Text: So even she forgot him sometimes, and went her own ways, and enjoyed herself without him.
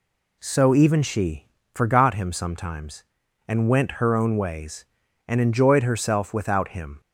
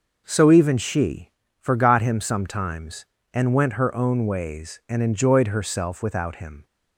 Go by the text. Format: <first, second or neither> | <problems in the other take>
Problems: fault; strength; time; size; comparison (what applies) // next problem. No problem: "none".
neither | pauses between "she" and "forgot"; slight; the same in both